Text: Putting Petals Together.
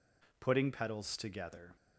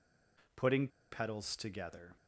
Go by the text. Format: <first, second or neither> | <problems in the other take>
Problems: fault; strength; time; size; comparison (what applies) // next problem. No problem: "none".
first | pauses between "Putting" and "Petals"; slight; at 0.8 s; 0.24 s long